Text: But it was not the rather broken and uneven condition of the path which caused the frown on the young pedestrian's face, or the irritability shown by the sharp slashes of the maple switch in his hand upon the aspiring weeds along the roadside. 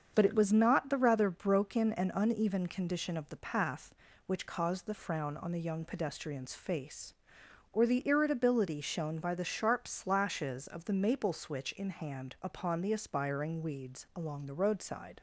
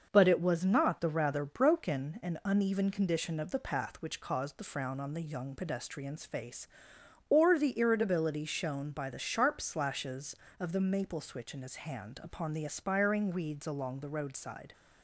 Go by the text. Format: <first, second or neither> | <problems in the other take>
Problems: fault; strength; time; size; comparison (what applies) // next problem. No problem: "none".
second | starts louder than the rest; strong; until 1.1 s; 7 dB; noticeable in the second // skips "his"; at 11.9 s